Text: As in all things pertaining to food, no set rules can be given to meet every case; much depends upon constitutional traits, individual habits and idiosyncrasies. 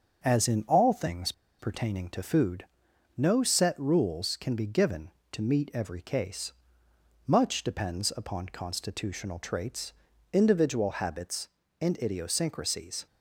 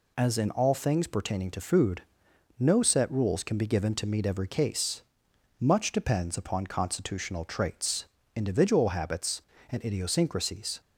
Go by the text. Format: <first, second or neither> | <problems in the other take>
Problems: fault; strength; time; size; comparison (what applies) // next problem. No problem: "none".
second | starts louder than the rest; until 1.2 s; 6.5 dB // pauses between "things" and "pertaining"; slight; at 1.3 s; 0.27 s long